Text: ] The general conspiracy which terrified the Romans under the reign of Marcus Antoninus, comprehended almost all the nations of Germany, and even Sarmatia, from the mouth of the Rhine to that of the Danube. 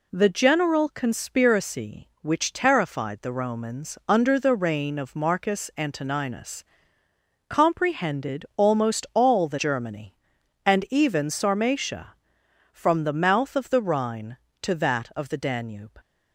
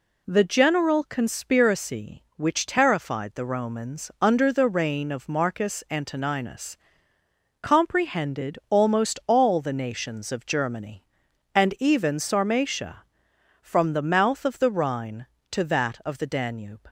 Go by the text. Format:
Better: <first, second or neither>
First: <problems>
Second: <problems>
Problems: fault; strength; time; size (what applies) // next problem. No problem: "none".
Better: second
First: skips "nations of"; at 9.5 s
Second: none